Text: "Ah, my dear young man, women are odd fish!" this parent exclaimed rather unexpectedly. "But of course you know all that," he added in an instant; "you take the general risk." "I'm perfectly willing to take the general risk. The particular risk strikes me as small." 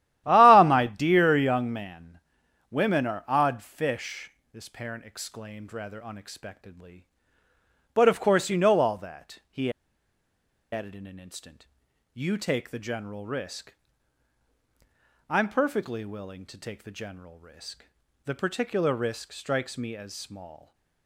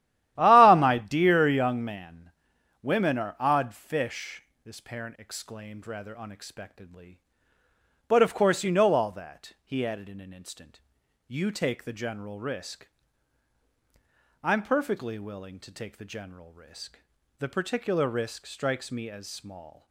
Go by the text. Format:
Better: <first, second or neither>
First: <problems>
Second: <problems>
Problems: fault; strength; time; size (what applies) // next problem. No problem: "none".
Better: second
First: starts louder than the rest; strong; until 1.2 s; 12.5 dB // pauses between "he" and "added"; at 9.7 s; 1.0 s long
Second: starts louder than the rest; strong; until 1.4 s; 12.5 dB